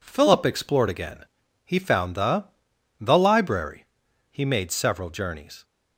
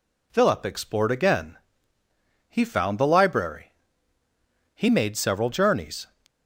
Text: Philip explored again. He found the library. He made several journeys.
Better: second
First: says "the" twice; at 2.9 s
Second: none

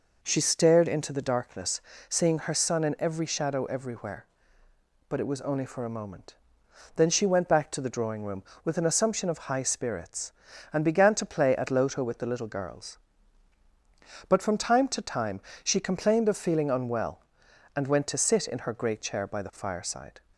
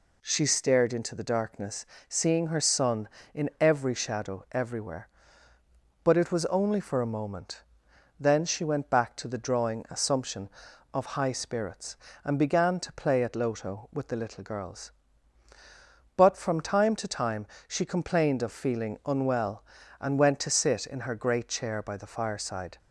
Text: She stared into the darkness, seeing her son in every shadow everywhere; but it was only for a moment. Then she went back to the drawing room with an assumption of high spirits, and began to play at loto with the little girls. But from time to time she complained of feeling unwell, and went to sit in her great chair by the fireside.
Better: first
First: pauses between "time" and "she"; slight; at 15.4 s; 0.24 s long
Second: skips "room with an"; at 9.8 s // pauses between "time" and "she"; slight; at 17.4 s; 0.22 s long

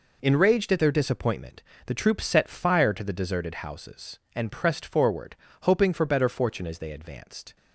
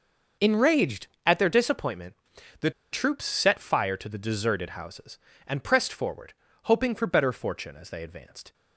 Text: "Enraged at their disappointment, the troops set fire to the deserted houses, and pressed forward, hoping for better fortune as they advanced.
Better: first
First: none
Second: pauses between "the" and "troops"; slight; at 2.6 s; 0.22 s long

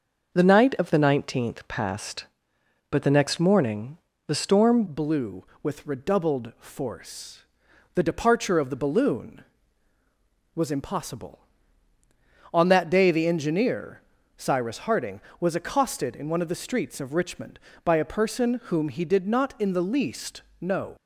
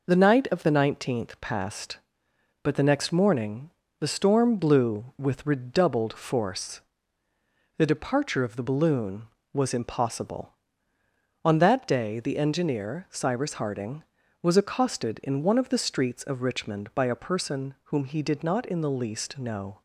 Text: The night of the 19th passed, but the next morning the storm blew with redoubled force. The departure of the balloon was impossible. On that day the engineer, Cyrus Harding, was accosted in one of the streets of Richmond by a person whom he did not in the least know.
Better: second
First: starts louder than the rest; noticeable; until 1.3 s; 6 dB // pauses between "morning" and "the"; slight; at 3.9 s; 0.30 s long // changes voice at "blew"; from 4.8 s on; 16.1 s long // pauses between "least" and "know"; slight; at 20.4 s; 0.18 s long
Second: pauses between "morning" and "the"; slight; at 3.7 s; 0.30 s long

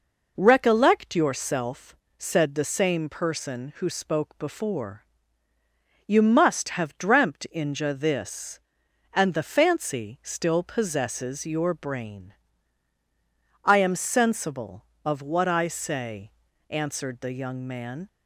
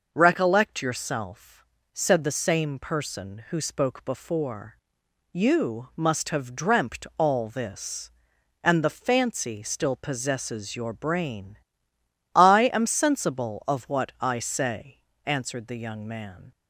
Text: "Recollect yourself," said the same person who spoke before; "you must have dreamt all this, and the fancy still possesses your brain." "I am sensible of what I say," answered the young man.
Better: second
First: says "inja" for "all"; at 7.5 s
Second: none

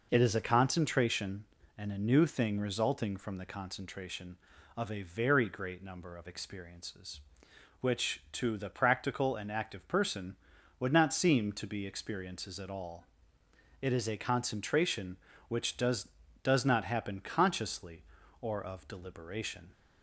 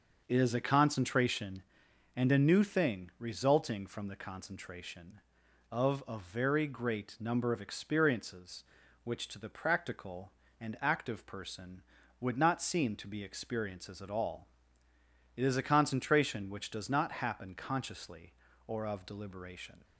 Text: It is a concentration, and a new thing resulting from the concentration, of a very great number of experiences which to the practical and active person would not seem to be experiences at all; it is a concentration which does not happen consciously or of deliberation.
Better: second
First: says "does" twice; at 16.4 s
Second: none

